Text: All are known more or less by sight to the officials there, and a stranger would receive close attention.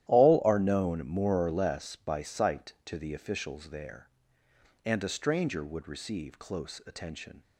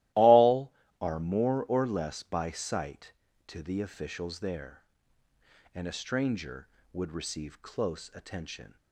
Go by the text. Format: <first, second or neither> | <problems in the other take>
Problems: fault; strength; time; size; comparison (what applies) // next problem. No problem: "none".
first | starts louder than the rest; strong; until 1.4 s; 16 dB; strong in the first // skips "known"; at 1.1 s